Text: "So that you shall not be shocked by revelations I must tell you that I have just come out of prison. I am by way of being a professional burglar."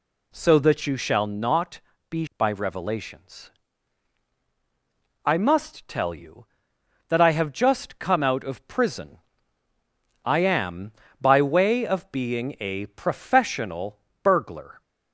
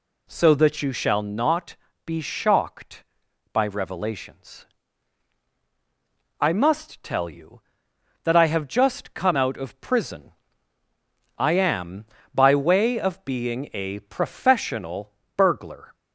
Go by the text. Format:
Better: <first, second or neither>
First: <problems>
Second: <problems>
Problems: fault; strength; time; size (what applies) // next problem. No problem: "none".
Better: second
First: pauses between "not" and "be"; slight; at 1.8 s; 0.28 s long // skips "shocked"; at 2.3 s // pauses between "revelations" and "I"; strong; at 3.5 s; 1.7 s long // pauses between "professional" and "burglar"; slight; at 13.9 s; 0.24 s long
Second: pauses between "not" and "be"; slight; at 1.7 s; 0.28 s long // pauses between "revelations" and "I"; strong; at 4.6 s; 1.7 s long // pauses between "professional" and "burglar"; slight; at 15.1 s; 0.24 s long